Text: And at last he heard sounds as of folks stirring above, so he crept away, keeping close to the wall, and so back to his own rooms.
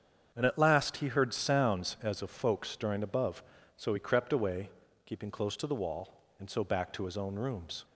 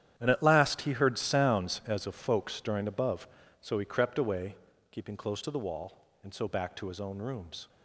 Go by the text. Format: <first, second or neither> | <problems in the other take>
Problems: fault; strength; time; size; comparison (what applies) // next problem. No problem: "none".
first | gets quieter; strong; throughout; 13 dB // starts louder than the rest; strong; until 1.1 s; 10 dB; strong in the first